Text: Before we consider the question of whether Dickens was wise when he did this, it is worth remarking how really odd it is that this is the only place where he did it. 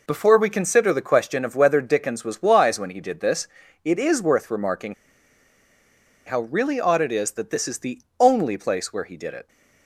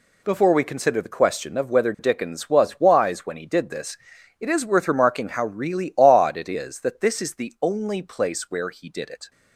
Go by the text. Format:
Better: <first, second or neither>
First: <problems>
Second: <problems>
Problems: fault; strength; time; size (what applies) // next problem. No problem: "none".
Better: second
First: pauses between "remarking" and "how"; strong; at 4.9 s; 1.3 s long // pauses between "the" and "only"; slight; at 7.9 s; 0.20 s long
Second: none